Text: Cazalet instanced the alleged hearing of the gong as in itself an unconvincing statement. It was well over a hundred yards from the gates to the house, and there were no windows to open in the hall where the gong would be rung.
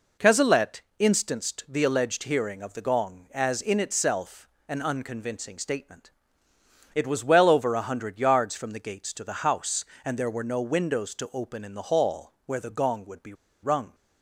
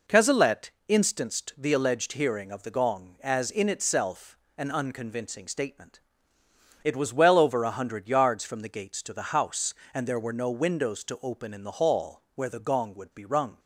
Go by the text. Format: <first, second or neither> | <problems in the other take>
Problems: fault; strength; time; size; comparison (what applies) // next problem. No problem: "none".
second | pauses between "Cazalet" and "instanced"; slight; at 0.8 s; 0.16 s long; slight in the second // pauses between "itself" and "an"; slight; at 4.4 s; 0.20 s long; slight in the second // pauses between "be" and "rung"; slight; at 13.3 s; 0.29 s long